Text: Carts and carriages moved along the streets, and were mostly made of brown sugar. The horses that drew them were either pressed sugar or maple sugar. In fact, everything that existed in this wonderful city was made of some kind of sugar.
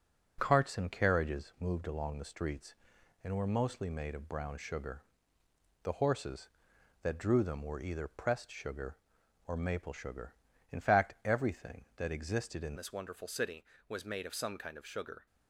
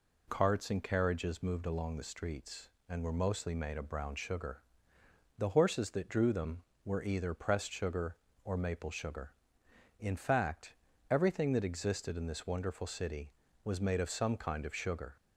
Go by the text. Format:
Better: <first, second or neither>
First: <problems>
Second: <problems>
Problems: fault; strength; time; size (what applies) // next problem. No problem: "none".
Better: second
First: changes voice at "this"; from 12.7 s on; 2.5 s long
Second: none